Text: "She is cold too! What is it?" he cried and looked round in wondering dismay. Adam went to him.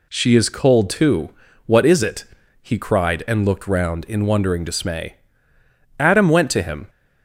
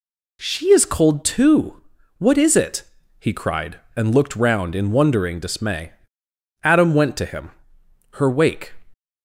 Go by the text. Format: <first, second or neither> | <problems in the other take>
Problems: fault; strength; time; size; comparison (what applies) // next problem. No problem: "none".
first | goes on to say "Her wake"; from 8.1 s on; 0.60 s long